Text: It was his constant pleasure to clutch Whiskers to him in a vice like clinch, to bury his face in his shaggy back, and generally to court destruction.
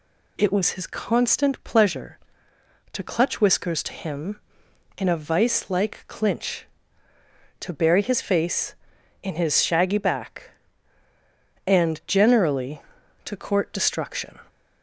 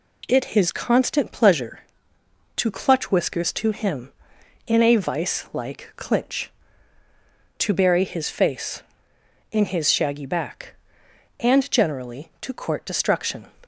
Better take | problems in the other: first | skips "was"; at 0.4 s

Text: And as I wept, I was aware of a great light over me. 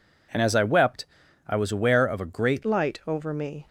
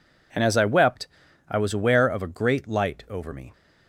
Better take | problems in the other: second | changes voice at "light"; from 2.6 s on; 1.0 s long

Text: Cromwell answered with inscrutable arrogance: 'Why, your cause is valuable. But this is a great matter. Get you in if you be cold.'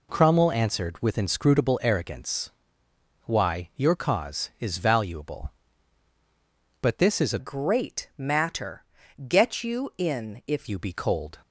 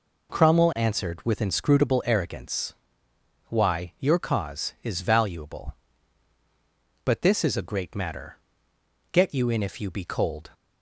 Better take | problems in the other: second | changes voice from "great" to "if"; from 7.3 to 10.6 s; 3.3 s long

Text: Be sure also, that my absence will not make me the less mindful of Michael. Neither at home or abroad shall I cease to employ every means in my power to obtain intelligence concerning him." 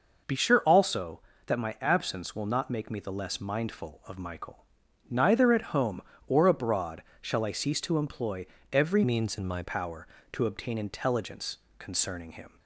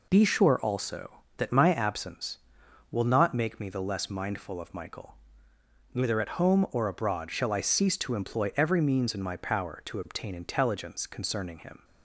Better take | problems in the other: second | pauses between "abroad" and "shall"; slight; at 7.0 s; 0.18 s long // pauses between "employ" and "every"; slight; at 8.4 s; 0.26 s long // changes voice from "means" to "my"; from 9.0 to 9.6 s; 0.6 s long // pauses between "intelligence" and "concerning"; slight; at 11.5 s; 0.18 s long

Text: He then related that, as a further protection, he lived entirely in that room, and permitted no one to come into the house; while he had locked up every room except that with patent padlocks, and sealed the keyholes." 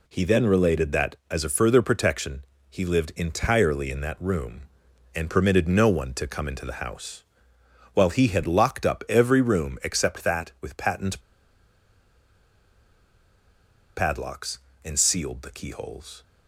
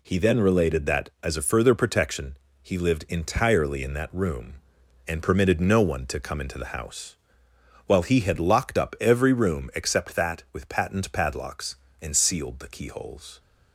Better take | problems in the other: second | pauses between "patent" and "padlocks"; strong; at 11.2 s; 2.7 s long

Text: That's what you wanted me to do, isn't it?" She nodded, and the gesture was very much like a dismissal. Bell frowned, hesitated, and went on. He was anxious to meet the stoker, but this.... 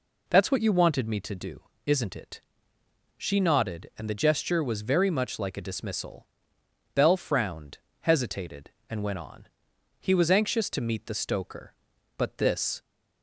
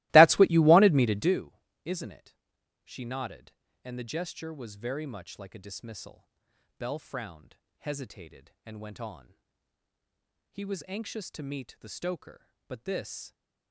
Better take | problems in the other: first | starts louder than the rest; strong; until 1.3 s; 20 dB

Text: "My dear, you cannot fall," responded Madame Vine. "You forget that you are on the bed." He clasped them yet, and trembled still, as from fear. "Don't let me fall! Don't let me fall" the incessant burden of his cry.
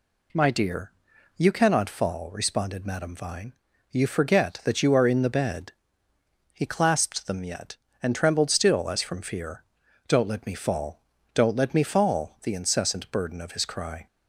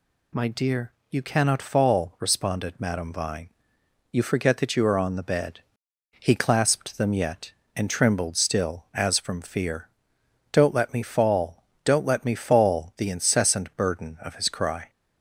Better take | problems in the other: second | says "in" for "on"; at 5.0 s

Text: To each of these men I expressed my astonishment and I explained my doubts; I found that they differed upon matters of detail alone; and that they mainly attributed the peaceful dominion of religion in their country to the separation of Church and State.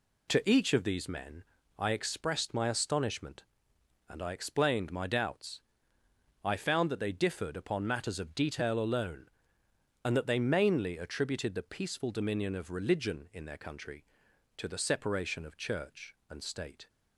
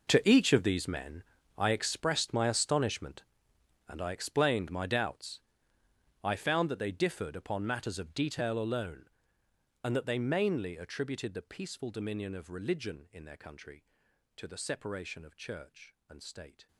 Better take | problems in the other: first | gets quieter; strong; throughout; 16.5 dB // pauses between "men" and "I"; slight; at 1.2 s; 0.34 s long; slight in the first

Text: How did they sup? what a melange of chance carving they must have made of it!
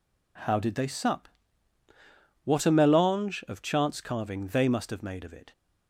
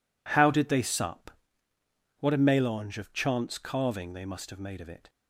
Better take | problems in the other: neither | none

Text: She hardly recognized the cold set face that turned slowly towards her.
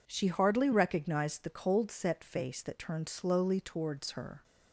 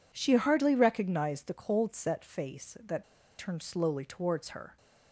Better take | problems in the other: first | pauses between "that" and "turned"; at 3.0 s; 0.36 s long

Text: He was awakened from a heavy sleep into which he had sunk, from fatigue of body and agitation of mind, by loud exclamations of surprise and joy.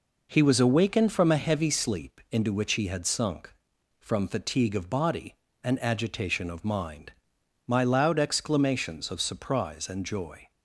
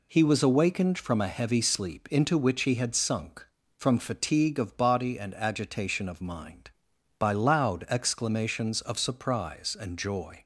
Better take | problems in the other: second | says "my" for "by"; at 7.6 s

